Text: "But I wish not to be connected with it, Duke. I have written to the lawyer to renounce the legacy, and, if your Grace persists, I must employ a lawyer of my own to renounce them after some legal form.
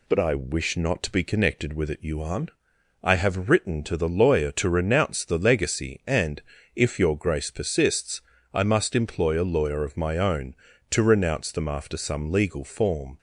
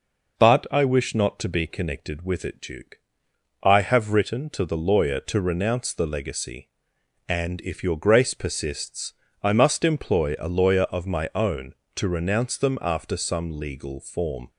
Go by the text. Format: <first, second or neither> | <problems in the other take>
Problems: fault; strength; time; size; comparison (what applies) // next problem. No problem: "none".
second | says "Yuan" for "Duke"; at 1.9 s